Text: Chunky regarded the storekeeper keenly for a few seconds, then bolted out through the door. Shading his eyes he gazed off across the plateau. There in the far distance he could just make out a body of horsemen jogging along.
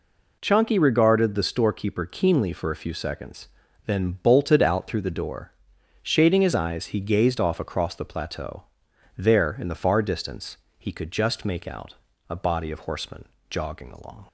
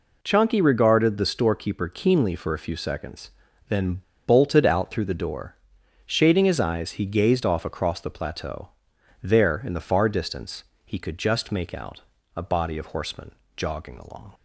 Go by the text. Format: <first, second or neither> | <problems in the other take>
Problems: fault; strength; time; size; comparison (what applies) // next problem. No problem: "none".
first | pauses between "then" and "bolted"; slight; at 4.0 s; 0.25 s long // pauses between "distance" and "he"; slight; at 10.6 s; 0.20 s long; slight in the first // pauses between "out" and "a"; slight; at 12.0 s; 0.34 s long; slight in the first // pauses between "horsemen" and "jogging"; slight; at 13.3 s; 0.24 s long; slight in the first